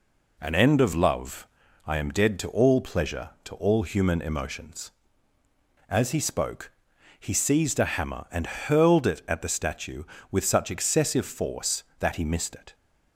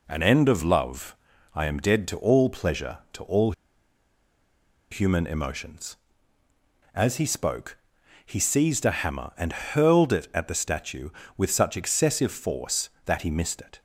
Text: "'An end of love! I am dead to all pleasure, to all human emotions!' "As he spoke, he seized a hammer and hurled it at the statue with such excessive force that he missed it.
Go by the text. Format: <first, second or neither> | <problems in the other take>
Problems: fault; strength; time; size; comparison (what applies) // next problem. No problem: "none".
first | pauses between "all" and "human"; strong; at 3.5 s; 1.3 s long